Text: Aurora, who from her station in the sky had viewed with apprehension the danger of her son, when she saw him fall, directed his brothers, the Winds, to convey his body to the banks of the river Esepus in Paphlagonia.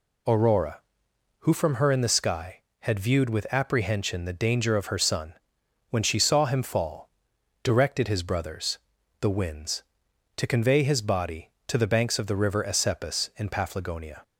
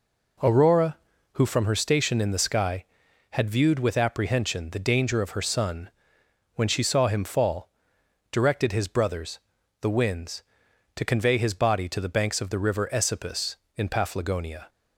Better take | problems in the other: second | skips "station"; at 1.9 s

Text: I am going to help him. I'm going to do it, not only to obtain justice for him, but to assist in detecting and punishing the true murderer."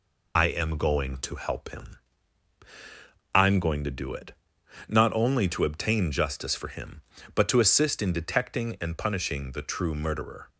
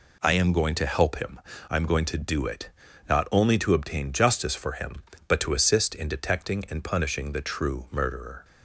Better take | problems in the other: second | loses the start of "I"; at 0.3 s; 40 ms

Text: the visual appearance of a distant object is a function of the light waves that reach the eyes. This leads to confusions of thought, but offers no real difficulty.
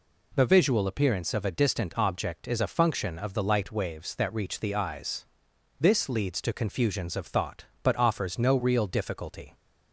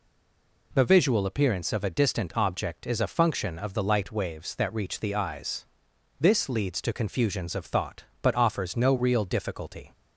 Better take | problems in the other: first | stays silent before the first word; slight; until 0.7 s; 0.7 s long

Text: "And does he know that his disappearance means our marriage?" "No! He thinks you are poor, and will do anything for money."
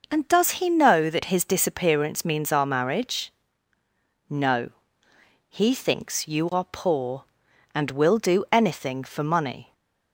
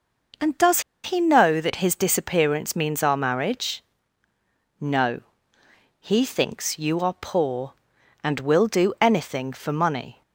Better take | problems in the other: first | pauses between "does" and "he"; slight; at 0.8 s; 0.23 s long

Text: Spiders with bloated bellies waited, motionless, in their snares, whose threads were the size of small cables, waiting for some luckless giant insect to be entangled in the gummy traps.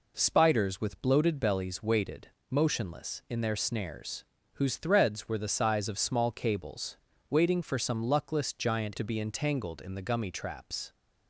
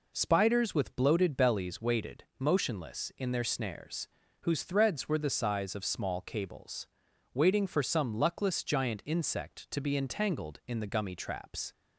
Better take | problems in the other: second | skips "insect"; at 8.9 s

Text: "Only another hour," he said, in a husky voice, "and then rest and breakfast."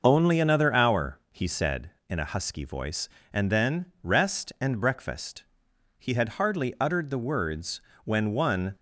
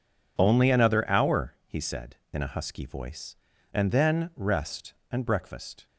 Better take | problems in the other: second | starts louder than the rest; noticeable; until 1.0 s; 6 dB // goes on to say "He had hardly uttered the words when one"; strong; from 5.9 s on; 2.7 s long

